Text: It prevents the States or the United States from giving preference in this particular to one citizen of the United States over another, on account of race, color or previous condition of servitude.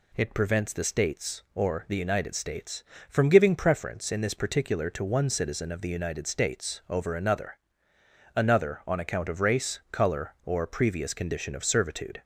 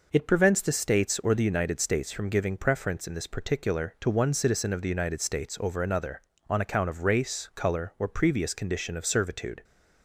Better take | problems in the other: second | says "another" twice; at 8.3 s

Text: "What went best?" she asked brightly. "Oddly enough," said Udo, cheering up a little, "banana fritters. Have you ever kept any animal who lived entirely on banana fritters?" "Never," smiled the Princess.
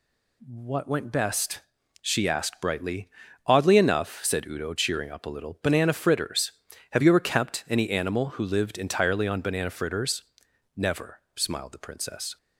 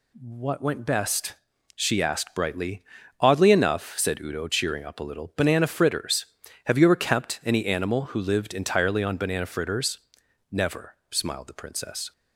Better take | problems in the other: neither | none

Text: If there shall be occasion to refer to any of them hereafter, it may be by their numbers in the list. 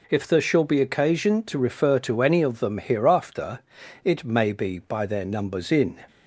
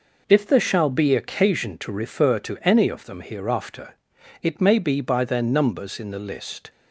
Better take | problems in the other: second | stops before "the list"; at 6.0 s

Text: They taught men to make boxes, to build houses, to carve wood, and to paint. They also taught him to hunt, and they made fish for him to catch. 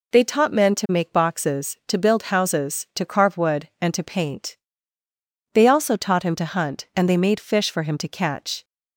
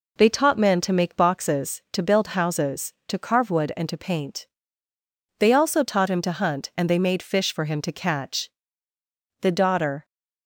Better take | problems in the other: first | goes on to say "The Daughter"; noticeable; from 9.4 s on; 0.64 s long

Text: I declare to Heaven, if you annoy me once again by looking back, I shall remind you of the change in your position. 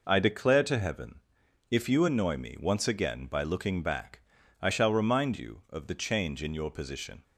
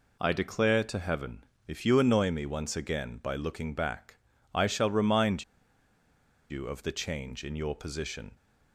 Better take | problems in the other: first | pauses between "remind" and "you"; at 5.4 s; 1.0 s long

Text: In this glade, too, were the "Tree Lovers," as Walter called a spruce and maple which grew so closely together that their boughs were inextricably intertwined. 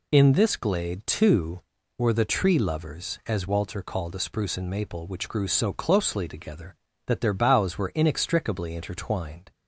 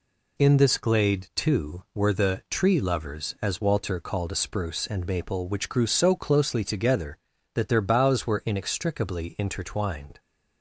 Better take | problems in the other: neither | none

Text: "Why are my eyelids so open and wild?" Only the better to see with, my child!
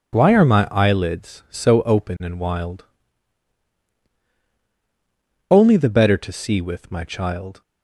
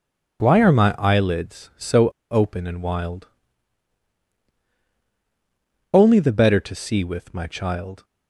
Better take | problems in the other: first | pauses between "so" and "open"; slight; at 2.0 s; 0.21 s long

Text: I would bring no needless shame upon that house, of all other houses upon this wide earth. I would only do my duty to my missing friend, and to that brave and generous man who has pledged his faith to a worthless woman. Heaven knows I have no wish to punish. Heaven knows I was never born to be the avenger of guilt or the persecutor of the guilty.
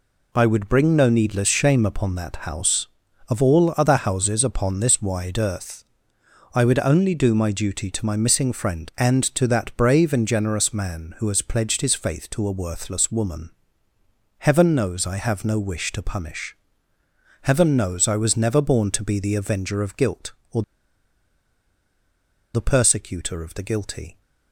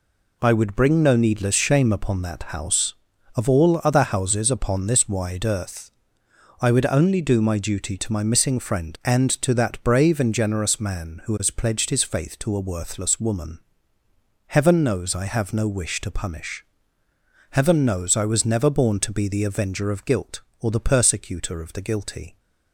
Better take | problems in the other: second | pauses between "or" and "the"; strong; at 20.6 s; 1.9 s long

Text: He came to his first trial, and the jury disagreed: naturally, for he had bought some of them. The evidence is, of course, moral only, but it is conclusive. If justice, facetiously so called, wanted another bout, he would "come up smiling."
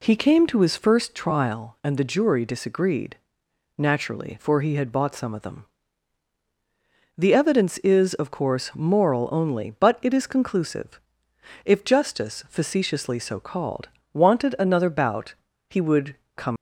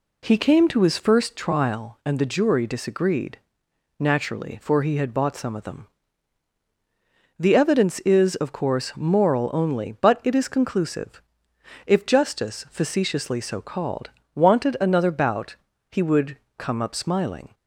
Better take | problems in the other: second | pauses between "would" and "come"; slight; at 16.1 s; 0.18 s long; slight in the second // stops before "up smiling"; at 16.5 s

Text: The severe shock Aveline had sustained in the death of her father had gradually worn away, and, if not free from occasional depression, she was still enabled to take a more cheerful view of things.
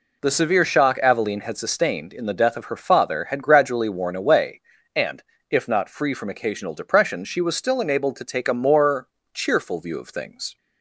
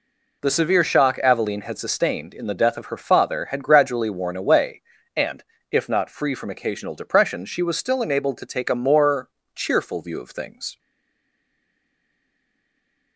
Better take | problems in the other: first | pauses between "more" and "cheerful"; slight; at 9.3 s; 0.26 s long; slight in the first // stays silent after the last word; from 10.7 s on; 2.4 s long

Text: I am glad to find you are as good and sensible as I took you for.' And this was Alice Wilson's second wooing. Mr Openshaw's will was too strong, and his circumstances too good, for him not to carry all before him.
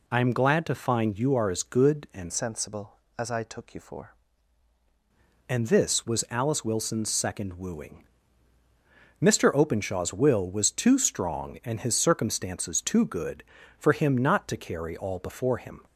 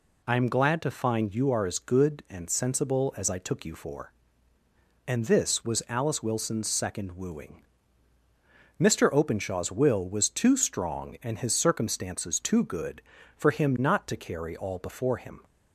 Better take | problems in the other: second | changes voice from "sensible" to "for"; from 2.2 to 4.1 s; 1.9 s long

